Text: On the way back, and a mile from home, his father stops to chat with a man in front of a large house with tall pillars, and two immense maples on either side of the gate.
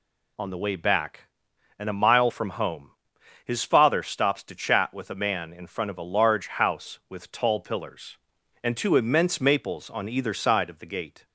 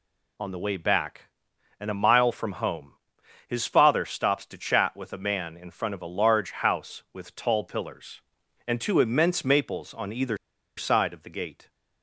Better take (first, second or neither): first